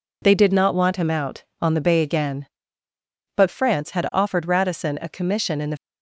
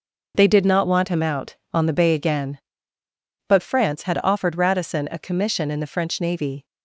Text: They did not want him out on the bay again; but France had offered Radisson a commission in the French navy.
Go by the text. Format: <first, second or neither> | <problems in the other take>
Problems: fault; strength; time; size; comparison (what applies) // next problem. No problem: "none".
second | stops before "French navy"; at 5.7 s